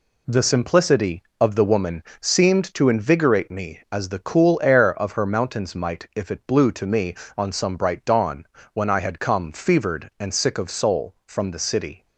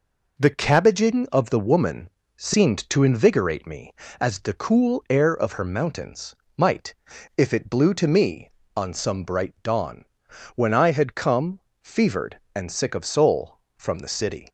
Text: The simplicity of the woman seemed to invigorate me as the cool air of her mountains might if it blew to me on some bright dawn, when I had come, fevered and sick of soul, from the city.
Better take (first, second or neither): first